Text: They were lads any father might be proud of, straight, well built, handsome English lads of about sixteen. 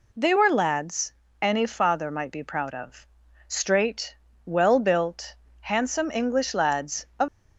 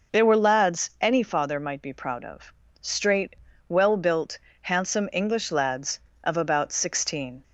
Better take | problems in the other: second | pauses between "lads" and "any"; slight; at 1.1 s; 0.28 s long // stops before "about sixteen"; at 7.2 s

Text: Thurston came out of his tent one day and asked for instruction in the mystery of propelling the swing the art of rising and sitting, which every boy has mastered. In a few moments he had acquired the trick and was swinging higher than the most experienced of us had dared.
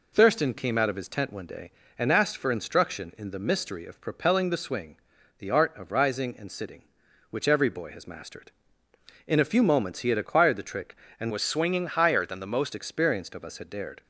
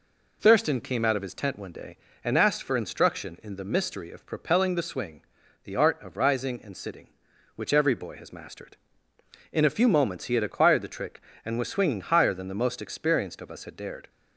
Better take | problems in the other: second | pauses between "swing" and "the"; at 4.9 s; 0.44 s long; also in the second // changes voice from "was" to "most"; from 11.3 to 12.7 s; 1.4 s long

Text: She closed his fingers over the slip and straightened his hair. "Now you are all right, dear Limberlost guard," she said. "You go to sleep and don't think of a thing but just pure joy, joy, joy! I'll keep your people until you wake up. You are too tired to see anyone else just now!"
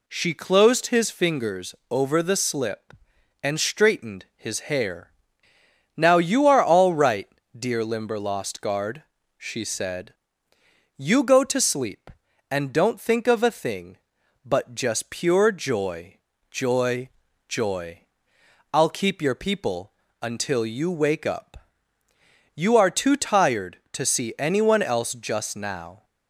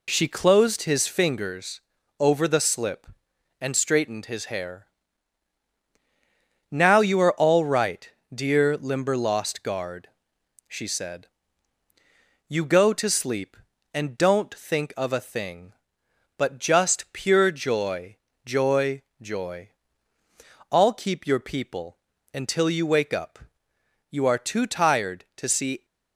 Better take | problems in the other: first | pauses between "fingers" and "over"; at 1.8 s; 0.38 s long; slight in the first // pauses between "people" and "until"; slight; at 21.9 s; 0.34 s long; slight in the first // stops before "anyone else just now"; at 25.8 s

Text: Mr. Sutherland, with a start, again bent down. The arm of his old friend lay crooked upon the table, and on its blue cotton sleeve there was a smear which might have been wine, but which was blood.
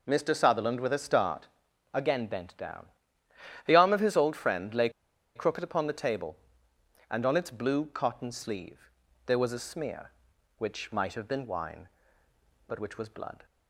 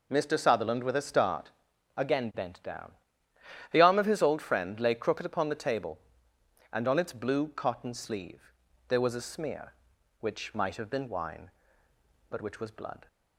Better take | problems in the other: second | pauses between "lay" and "crooked"; noticeable; at 4.8 s; 0.46 s long // pauses between "sleeve" and "there"; slight; at 8.9 s; 0.34 s long; slight in the second

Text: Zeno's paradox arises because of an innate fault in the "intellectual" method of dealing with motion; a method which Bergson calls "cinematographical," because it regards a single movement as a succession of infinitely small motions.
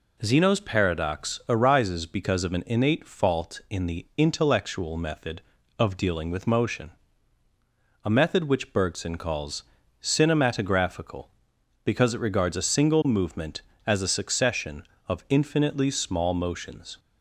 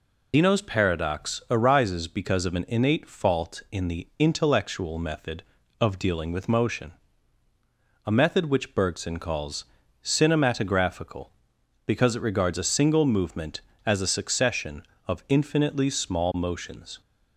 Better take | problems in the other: first | loses the start of "Zeno's"; at 0.3 s; 125 ms // pauses between "calls" and "cinematographical"; at 9.6 s; 0.40 s long; also in the first

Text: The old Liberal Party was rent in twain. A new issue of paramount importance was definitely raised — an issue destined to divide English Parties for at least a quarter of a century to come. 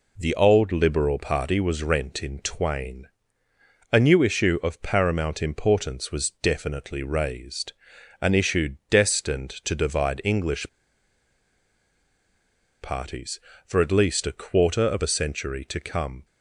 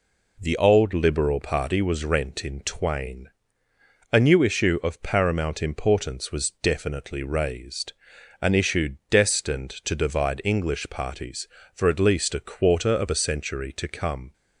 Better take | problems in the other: second | pauses between "English" and "Parties"; strong; at 10.6 s; 2.1 s long

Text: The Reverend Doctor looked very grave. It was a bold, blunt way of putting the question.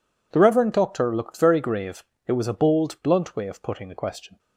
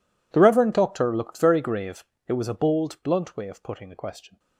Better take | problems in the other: first | gets quieter; strong; throughout; 24 dB

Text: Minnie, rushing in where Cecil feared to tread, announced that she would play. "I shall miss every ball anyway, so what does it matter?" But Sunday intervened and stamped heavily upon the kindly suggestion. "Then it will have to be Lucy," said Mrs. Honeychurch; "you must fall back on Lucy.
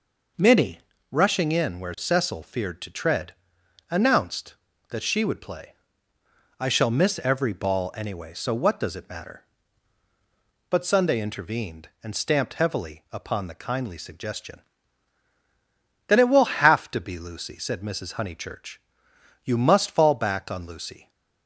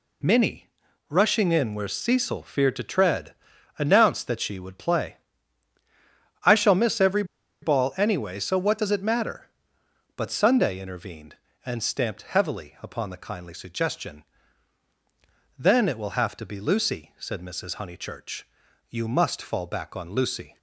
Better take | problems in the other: first | pauses between "every" and "ball"; at 7.2 s; 0.38 s long

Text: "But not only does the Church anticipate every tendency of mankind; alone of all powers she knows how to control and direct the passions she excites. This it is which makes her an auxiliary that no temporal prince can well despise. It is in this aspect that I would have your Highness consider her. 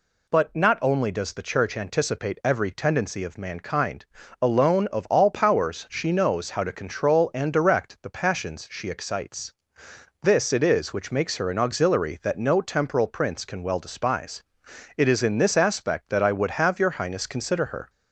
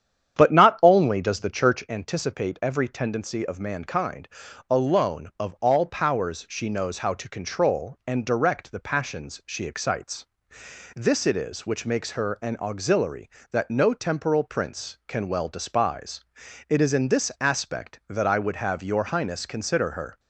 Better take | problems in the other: first | starts louder than the rest; strong; until 2.0 s; 9 dB

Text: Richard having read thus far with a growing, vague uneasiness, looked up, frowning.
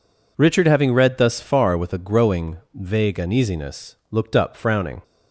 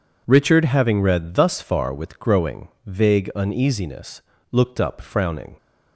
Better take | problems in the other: first | skips "a"; at 2.1 s

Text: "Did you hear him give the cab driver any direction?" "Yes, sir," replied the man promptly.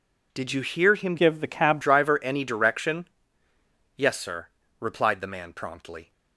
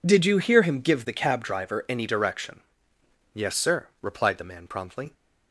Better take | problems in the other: second | changes voice from "give" to "cab"; from 1.1 to 1.7 s; 0.6 s long

